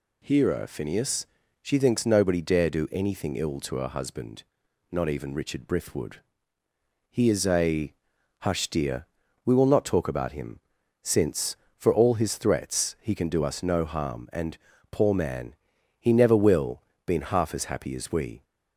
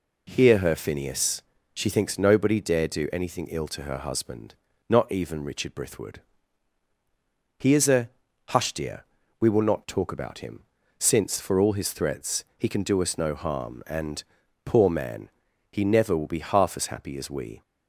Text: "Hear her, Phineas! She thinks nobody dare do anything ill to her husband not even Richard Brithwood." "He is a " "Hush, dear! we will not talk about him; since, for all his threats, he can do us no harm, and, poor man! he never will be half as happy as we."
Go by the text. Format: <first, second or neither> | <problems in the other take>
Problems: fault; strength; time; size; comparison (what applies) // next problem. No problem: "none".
second | pauses between "husband" and "not"; at 4.4 s; 0.44 s long; slight in the second // says "been" for "be"; at 17.0 s